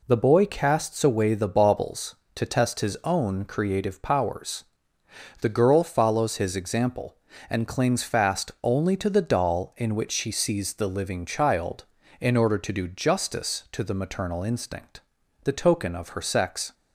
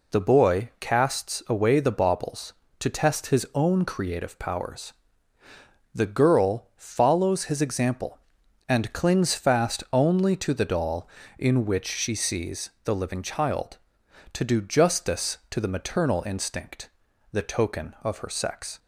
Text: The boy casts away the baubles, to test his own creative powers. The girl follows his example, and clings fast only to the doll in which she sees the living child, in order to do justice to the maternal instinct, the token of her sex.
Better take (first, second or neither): first